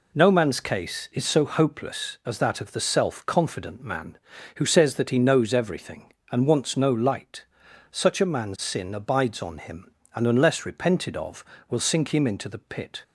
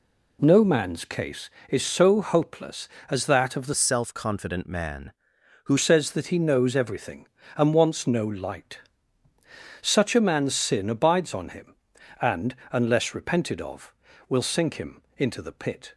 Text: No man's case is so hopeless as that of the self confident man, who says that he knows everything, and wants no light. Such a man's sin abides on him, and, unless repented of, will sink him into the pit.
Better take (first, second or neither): first